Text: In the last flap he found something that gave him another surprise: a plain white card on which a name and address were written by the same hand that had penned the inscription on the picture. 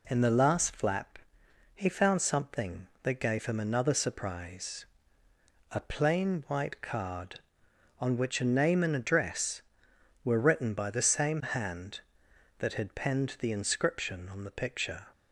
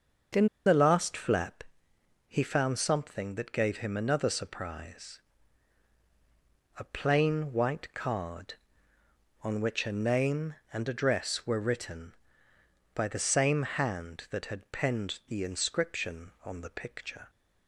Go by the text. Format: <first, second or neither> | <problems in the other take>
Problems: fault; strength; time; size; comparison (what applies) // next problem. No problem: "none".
first | starts louder than the rest; until 1.5 s; 6.5 dB // pauses between "In" and "the"; slight; at 0.4 s; 0.18 s long // pauses between "flap" and "he"; noticeable; at 1.6 s; 0.64 s long; noticeable in the first